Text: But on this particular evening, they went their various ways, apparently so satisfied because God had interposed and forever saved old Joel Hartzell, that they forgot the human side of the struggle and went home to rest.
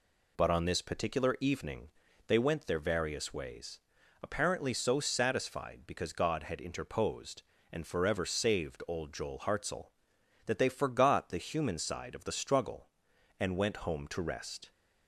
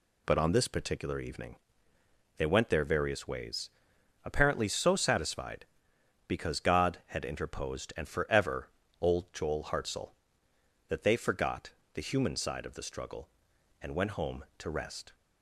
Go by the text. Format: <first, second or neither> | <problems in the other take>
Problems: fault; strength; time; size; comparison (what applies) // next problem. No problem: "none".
first | skips "saved"; at 8.8 s // pauses between "forgot" and "the"; slight; at 11.7 s; 0.22 s long